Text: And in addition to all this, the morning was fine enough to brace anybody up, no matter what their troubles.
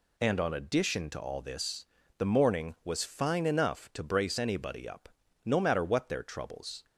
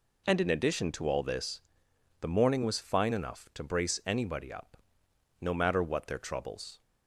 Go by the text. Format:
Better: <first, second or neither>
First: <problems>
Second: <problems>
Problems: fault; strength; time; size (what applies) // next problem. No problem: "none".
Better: second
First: says "on" for "in"; at 0.3 s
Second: none